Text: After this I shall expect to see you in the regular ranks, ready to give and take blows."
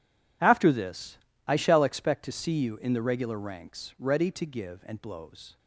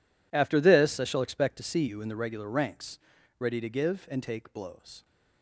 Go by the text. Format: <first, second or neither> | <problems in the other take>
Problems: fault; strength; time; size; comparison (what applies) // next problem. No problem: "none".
second | pauses between "this" and "I"; slight; at 1.1 s; 0.30 s long // skips "take"; at 5.0 s